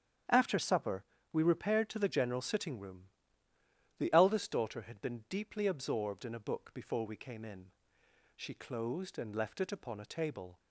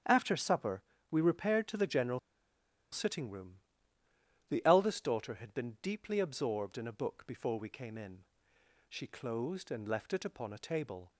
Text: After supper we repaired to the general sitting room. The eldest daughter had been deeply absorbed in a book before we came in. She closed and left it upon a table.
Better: first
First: starts louder than the rest; strong; until 1.5 s; 9 dB // pauses between "supper" and "we"; slight; at 1.0 s; 0.30 s long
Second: starts louder than the rest; strong; until 1.3 s; 9 dB // pauses between "supper" and "we"; slight; at 0.8 s; 0.30 s long // pauses between "general" and "sitting"; noticeable; at 2.1 s; 0.73 s long

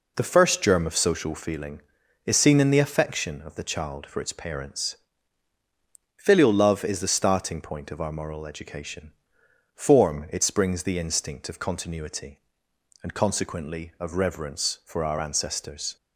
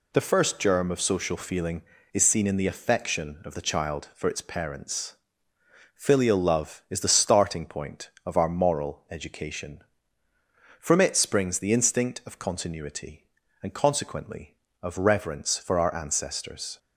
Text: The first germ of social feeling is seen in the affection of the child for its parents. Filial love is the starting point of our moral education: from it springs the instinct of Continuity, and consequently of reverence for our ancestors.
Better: second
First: says "form" for "from"; at 9.7 s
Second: none

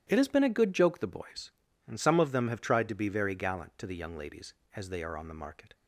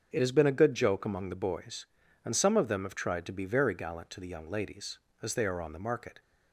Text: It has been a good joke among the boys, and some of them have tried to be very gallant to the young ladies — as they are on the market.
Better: second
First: starts louder than the rest; strong; until 1.0 s; 10.5 dB // skips "among"; at 1.0 s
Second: starts louder than the rest; until 1.1 s; 7 dB

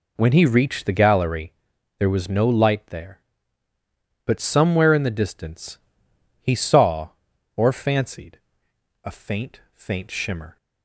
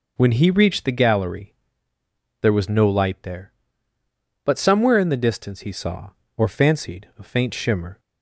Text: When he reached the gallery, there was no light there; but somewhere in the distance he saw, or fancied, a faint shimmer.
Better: second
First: pauses between "distance" and "he"; noticeable; at 5.7 s; 0.64 s long // says "faint" twice; at 9.7 s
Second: none

